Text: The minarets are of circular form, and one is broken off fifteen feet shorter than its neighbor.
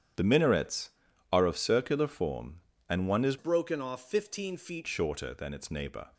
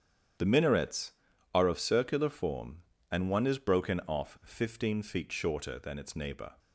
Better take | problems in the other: second | starts louder than the rest; strong; until 1.6 s; 9 dB; strong in the second // changes voice from "broken" to "feet"; from 3.3 to 4.8 s; 1.5 s long

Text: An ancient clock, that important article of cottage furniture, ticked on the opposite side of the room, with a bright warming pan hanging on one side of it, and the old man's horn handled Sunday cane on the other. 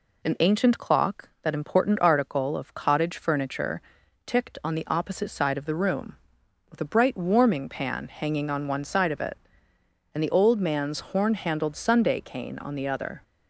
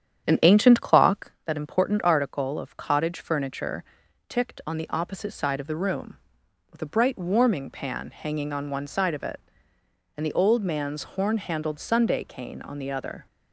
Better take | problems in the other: first | starts louder than the rest; strong; until 1.4 s; 9 dB

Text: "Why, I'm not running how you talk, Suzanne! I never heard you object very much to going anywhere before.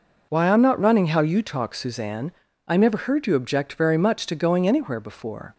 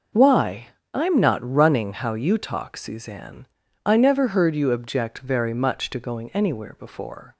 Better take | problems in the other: neither | none

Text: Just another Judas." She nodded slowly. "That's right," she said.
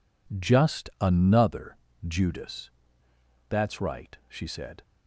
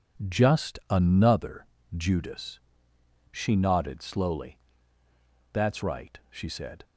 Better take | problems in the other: second | pauses between "another" and "Judas"; slight; at 1.7 s; 0.28 s long; slight in the second // skips "She nodded slowly"; at 3.0 s

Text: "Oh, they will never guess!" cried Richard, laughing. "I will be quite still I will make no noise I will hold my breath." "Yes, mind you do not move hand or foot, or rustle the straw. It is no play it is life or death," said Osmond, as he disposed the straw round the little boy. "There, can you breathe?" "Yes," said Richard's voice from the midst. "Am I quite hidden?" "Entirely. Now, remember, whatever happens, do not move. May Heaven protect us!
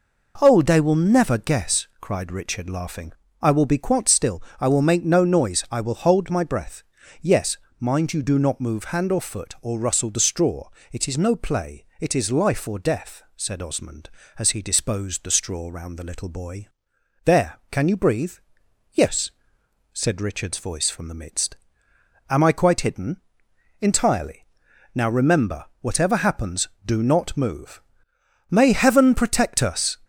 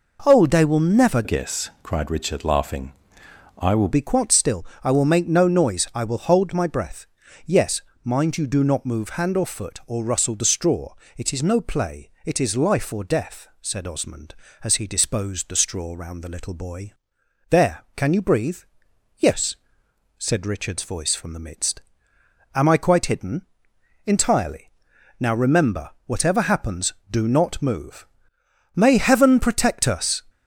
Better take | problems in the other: first | changes voice from "guess" to "will"; from 1.2 to 3.8 s; 2.6 s long // pauses between "still" and "I"; slight; at 4.6 s; 0.18 s long; slight in the first // pauses between "play" and "it"; slight; at 12.0 s; 0.16 s long; slight in the first

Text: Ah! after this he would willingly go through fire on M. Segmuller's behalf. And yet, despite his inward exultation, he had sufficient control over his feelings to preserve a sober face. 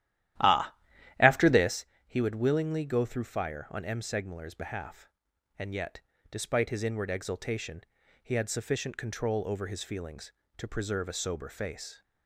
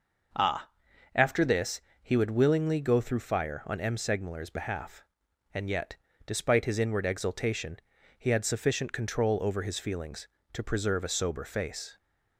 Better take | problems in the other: second | starts louder than the rest; strong; until 1.8 s; 12.5 dB // pauses between "this" and "he"; slight; at 1.8 s; 0.20 s long; slight in the second

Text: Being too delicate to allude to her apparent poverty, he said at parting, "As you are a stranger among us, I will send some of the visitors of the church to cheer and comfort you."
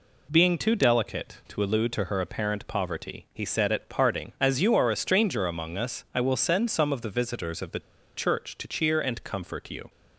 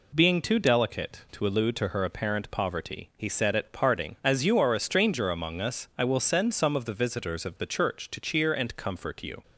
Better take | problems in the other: second | pauses between "the" and "church"; at 7.7 s; 0.36 s long

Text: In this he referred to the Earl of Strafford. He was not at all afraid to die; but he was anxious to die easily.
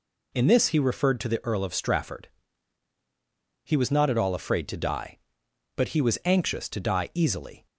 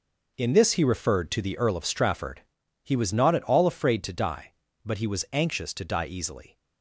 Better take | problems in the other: first | gets quieter; strong; throughout; 10 dB

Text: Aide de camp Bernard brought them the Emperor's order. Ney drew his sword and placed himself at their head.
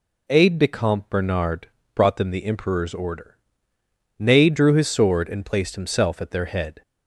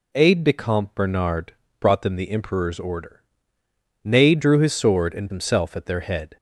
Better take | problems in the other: first | pauses between "Bernard" and "brought"; slight; at 1.5 s; 0.26 s long; slight in the first // skips "placed"; at 5.3 s

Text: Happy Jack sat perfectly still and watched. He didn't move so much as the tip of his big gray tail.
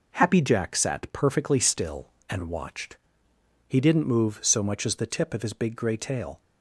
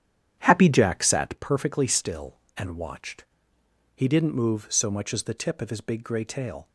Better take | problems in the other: first | starts louder than the rest; strong; until 1.4 s; 9.5 dB

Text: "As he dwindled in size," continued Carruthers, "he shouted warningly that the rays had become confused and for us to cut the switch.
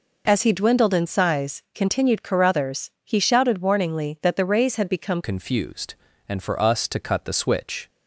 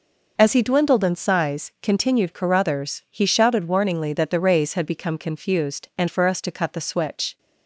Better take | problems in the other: second | changes voice at "confused"; from 5.2 s on; 2.6 s long

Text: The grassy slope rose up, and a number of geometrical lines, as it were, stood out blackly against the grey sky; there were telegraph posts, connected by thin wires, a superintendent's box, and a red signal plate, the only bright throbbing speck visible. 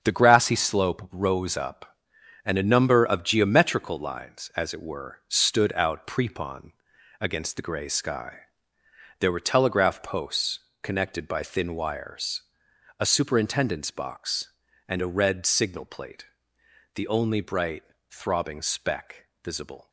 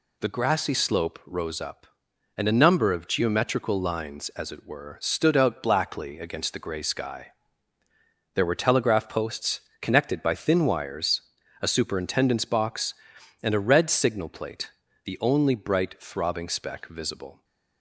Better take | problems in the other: second | starts louder than the rest; until 1.0 s; 6.5 dB // says "prepon" for "blackly"; at 6.0 s // pauses between "bright" and "throbbing"; slight; at 17.8 s; 0.26 s long // pauses between "speck" and "visible"; slight; at 19.2 s; 0.16 s long

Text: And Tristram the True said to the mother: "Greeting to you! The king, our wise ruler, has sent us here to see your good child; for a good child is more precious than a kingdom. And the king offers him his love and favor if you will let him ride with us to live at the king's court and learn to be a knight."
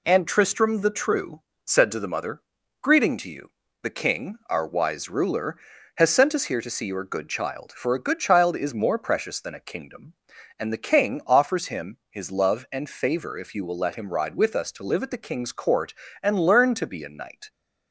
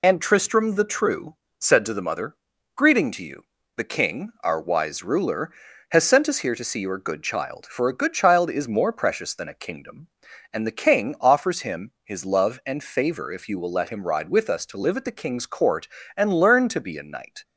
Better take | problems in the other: first | loses the start of "And"; at 0.0 s; 35 ms // pauses between "True" and "said"; slight; at 1.3 s; 0.24 s long; slight in the first

